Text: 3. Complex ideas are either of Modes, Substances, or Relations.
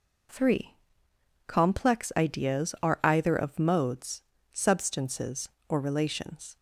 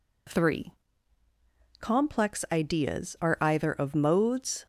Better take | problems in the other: first | stops before "Substances or Relations"; at 4.6 s

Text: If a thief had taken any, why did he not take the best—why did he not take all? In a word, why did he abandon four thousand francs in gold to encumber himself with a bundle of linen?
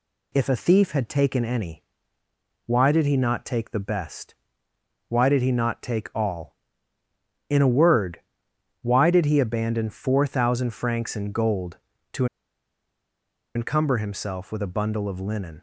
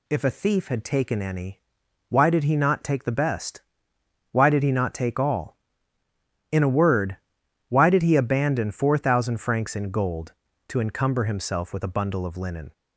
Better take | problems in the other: second | pauses between "to" and "encumber"; strong; at 12.2 s; 1.3 s long

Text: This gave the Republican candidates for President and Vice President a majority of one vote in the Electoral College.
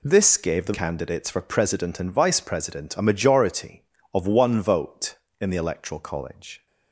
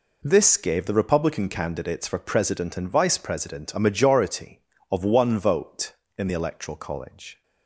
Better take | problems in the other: second | skips "Republican"; at 0.7 s

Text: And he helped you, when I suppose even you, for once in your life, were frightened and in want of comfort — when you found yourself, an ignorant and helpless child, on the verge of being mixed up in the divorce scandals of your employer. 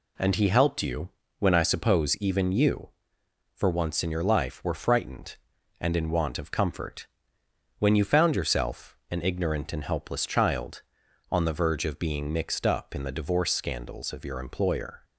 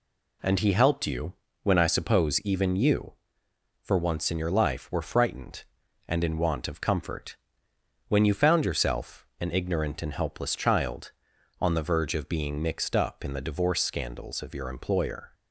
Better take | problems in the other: neither | none

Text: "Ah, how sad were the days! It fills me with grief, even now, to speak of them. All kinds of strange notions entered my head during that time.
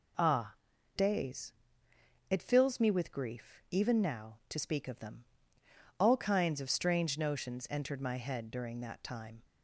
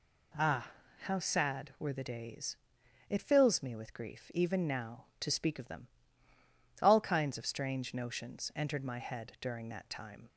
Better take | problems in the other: second | skips "how sad were the"; at 0.7 s

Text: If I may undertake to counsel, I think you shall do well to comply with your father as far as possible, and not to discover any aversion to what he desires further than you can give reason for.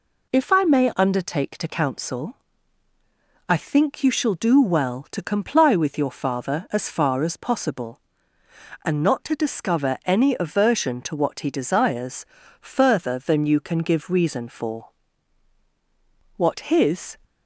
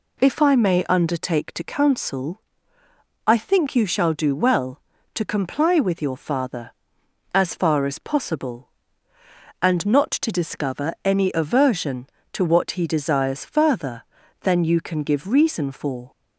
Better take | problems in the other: second | pauses between "desires" and "further"; slight; at 12.2 s; 0.34 s long // goes on to say "What his"; noticeable; from 16.3 s on; 0.82 s long

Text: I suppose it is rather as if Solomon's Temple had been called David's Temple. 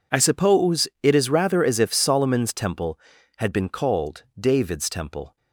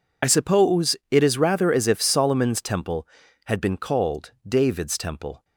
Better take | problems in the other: first | loses the start of "I"; at 0.2 s; 30 ms // pauses between "suppose" and "it"; slight; at 0.9 s; 0.16 s long; slight in the first // pauses between "called" and "David's"; slight; at 4.3 s; 0.16 s long; slight in the first

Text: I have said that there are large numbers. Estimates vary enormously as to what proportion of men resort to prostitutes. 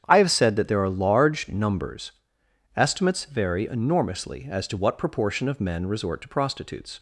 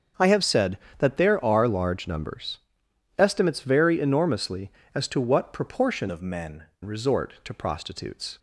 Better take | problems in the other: first | starts louder than the rest; until 1.3 s; 7 dB; strong in the first // changes voice from "of" to "men"; from 6.0 to 6.6 s; 0.6 s long

